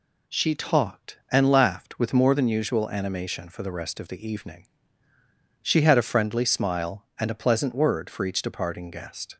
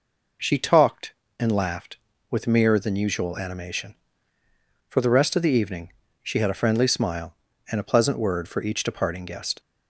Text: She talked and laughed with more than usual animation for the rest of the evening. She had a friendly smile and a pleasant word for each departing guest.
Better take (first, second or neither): first